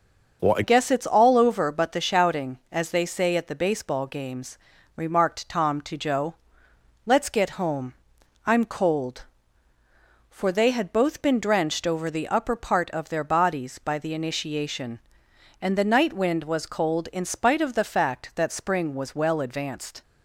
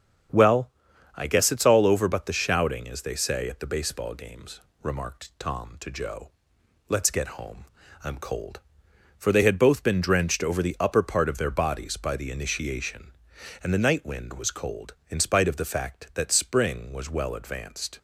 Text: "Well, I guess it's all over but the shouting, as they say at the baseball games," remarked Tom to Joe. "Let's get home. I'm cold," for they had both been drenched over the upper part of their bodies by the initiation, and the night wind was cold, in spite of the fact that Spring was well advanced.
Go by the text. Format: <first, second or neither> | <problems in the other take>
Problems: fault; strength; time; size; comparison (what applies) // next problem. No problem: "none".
second | starts louder than the rest; until 1.4 s; 6.5 dB; strong in the second // changes voice at "guess"; from 0.6 s on; 19.4 s long